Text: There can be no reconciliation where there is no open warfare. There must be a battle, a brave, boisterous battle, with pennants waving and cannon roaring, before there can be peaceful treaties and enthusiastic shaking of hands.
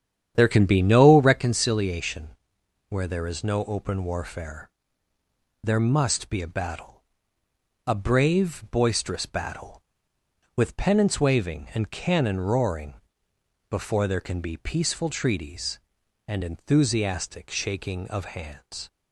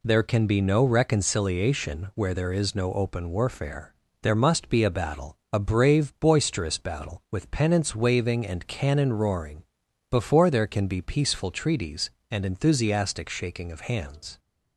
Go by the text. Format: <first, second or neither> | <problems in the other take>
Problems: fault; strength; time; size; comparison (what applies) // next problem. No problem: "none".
second | starts louder than the rest; strong; until 1.4 s; 9 dB // pauses between "reconciliation" and "where"; noticeable; at 2.2 s; 0.62 s long